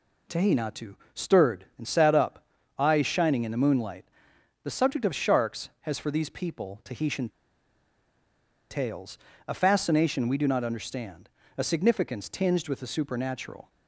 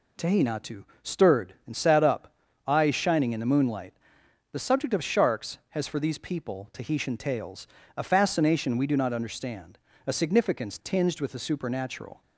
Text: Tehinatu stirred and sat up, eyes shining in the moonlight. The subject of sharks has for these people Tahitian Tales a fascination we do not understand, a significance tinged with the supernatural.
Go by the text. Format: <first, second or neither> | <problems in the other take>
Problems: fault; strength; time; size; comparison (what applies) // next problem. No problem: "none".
second | pauses between "Tehinatu" and "stirred"; slight; at 0.9 s; 0.18 s long; slight in the second // pauses between "Tahitian" and "Tales"; strong; at 7.2 s; 1.4 s long // pauses between "Tales" and "a"; slight; at 9.1 s; 0.30 s long; slight in the second